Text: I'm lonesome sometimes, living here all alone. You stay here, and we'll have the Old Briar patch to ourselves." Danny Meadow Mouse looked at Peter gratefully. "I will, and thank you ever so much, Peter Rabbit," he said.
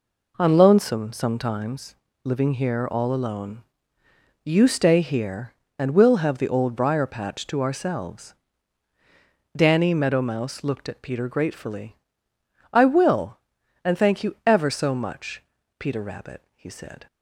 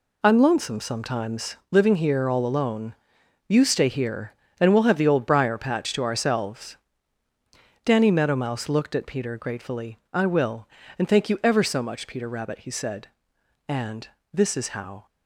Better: first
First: none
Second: goes on to say "And this is how"; from 13.6 s on; 1.3 s long

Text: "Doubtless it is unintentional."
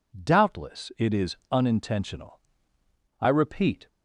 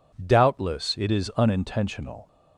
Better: second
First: pauses between "is" and "unintentional"; slight; at 1.3 s; 0.16 s long // goes on to say "I repeat"; noticeable; from 3.2 s on; 0.67 s long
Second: none

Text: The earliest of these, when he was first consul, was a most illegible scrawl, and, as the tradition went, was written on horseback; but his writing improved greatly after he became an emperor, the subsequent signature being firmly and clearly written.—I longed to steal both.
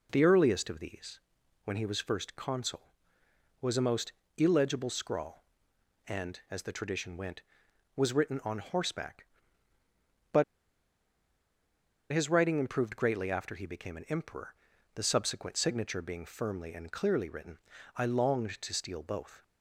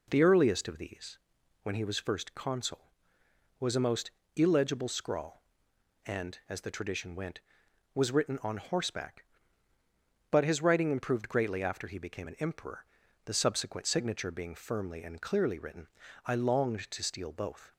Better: second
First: pauses between "most" and "illegible"; slight; at 4.1 s; 0.26 s long // pauses between "but" and "his"; strong; at 10.4 s; 1.6 s long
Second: pauses between "most" and "illegible"; slight; at 4.0 s; 0.26 s long

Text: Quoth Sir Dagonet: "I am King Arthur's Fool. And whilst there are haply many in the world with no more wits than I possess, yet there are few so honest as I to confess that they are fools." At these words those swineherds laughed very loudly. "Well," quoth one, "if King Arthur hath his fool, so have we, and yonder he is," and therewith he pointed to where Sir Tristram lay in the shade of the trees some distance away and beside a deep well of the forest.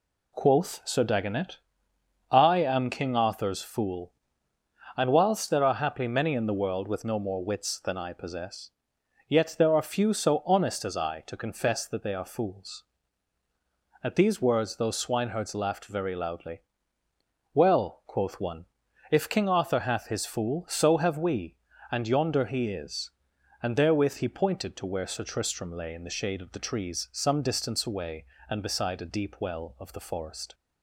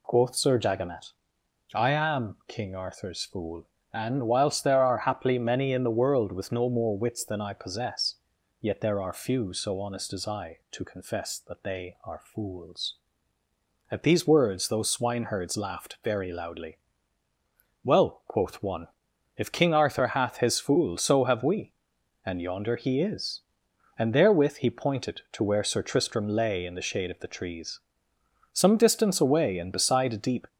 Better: first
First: none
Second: pauses between "trees" and "some"; noticeable; at 27.7 s; 0.72 s long // stops before "well of the forest"; at 30.4 s

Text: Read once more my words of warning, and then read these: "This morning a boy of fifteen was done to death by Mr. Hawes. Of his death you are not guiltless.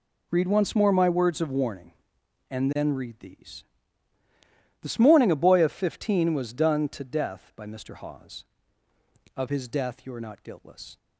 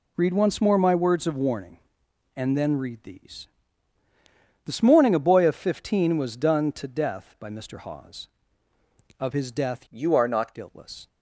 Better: first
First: none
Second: changes voice from "you" to "not"; from 9.8 to 10.5 s; 0.7 s long

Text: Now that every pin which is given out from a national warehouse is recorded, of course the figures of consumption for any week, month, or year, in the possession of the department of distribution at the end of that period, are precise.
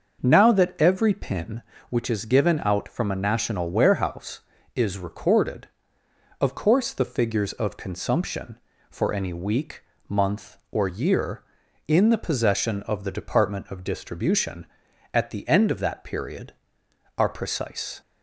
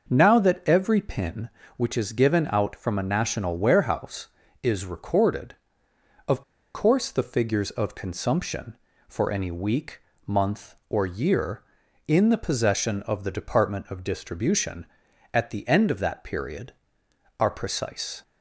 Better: first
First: starts louder than the rest; until 1.2 s; 6.5 dB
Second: starts louder than the rest; noticeable; until 1.1 s; 6 dB // pauses between "of" and "course"; slight; at 6.4 s; 0.33 s long

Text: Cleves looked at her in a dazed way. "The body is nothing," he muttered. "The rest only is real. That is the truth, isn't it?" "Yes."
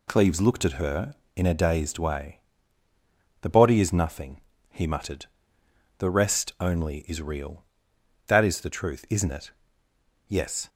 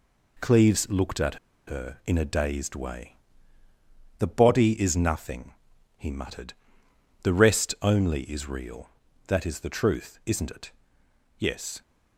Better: first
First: none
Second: pauses between "at" and "her"; slight; at 1.3 s; 0.31 s long

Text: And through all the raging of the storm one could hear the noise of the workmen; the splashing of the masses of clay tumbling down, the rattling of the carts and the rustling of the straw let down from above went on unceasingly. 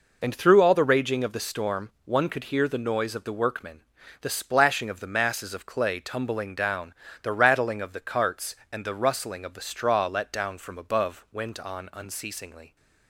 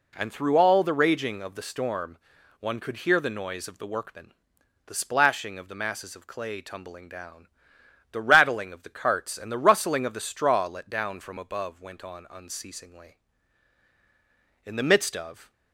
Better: first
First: none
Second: pauses between "storm" and "one"; at 2.1 s; 0.42 s long // goes on to say "In the midst of"; noticeable; from 14.6 s on; 0.88 s long

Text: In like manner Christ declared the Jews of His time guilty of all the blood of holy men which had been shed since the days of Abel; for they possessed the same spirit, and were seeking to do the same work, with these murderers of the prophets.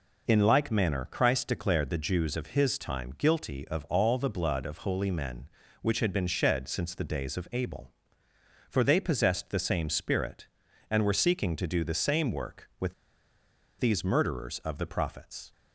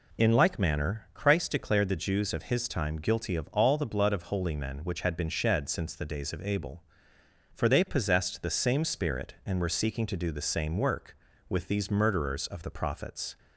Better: second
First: pauses between "with" and "these"; noticeable; at 12.9 s; 0.87 s long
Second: none

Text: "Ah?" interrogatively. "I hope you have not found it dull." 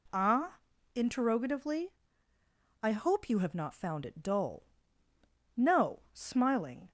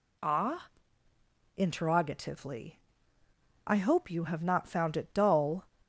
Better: second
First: goes on to say "No smiling"; from 5.5 s on; 1.3 s long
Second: none

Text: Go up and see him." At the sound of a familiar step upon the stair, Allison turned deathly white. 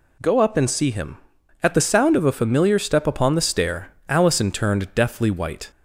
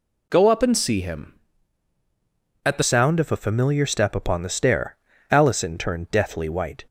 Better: first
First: none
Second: changes voice at "sound"; from 2.8 s on; 4.0 s long

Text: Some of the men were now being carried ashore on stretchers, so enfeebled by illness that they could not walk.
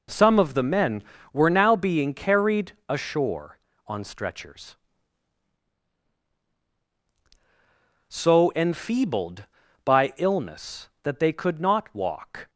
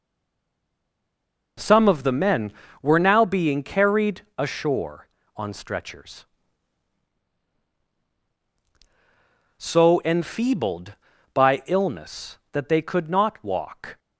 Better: first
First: pauses between "carried" and "ashore"; slight; at 2.7 s; 0.18 s long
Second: stays silent before the first word; noticeable; until 1.5 s; 1.5 s long // pauses between "carried" and "ashore"; slight; at 4.2 s; 0.18 s long

